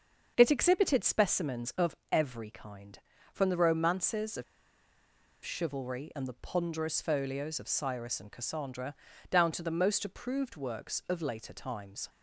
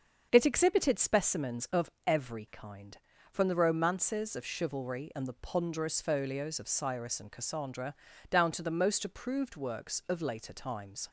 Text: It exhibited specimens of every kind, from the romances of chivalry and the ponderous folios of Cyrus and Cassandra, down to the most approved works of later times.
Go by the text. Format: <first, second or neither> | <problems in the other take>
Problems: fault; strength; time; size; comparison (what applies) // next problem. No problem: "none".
second | starts louder than the rest; until 1.3 s; 7 dB; also in the second // pauses between "of" and "every"; slight; at 1.9 s; 0.16 s long; slight in the second // pauses between "of" and "chivalry"; at 4.4 s; 0.99 s long